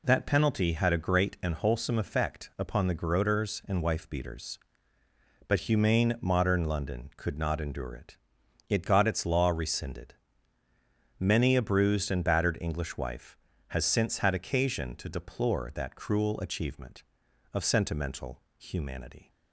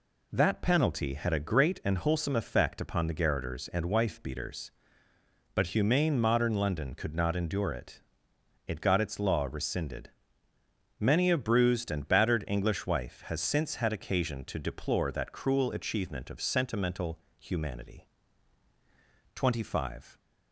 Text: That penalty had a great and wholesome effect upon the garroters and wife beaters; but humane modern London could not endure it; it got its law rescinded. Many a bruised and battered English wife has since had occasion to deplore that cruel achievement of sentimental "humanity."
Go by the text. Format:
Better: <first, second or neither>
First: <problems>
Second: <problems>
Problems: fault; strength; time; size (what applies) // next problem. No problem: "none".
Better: first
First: pauses between "sentimental" and "humanity"; slight; at 18.4 s; 0.16 s long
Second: pauses between "sentimental" and "humanity"; slight; at 17.1 s; 0.20 s long // goes on to say "Twenty five"; noticeable; from 19.3 s on; 0.84 s long